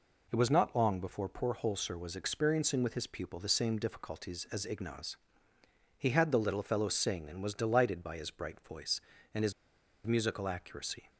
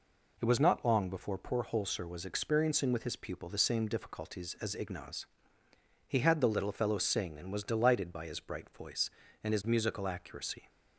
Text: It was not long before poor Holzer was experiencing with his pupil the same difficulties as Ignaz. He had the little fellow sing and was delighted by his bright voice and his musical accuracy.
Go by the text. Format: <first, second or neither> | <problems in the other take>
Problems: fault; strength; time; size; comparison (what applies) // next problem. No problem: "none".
second | pauses between "his" and "musical"; noticeable; at 9.5 s; 0.54 s long